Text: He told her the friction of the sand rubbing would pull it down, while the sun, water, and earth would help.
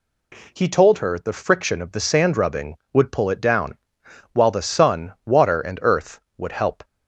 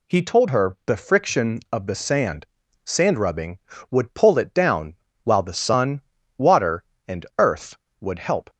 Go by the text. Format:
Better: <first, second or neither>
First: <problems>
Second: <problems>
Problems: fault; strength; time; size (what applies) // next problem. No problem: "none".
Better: first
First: none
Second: says "sand" twice; at 2.8 s